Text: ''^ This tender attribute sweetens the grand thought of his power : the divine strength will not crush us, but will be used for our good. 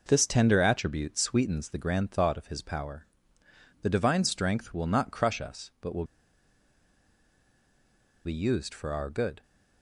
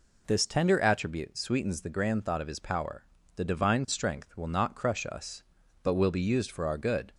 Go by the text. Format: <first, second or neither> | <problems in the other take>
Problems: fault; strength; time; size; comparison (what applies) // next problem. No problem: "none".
second | pauses between "will" and "be"; strong; at 6.0 s; 2.2 s long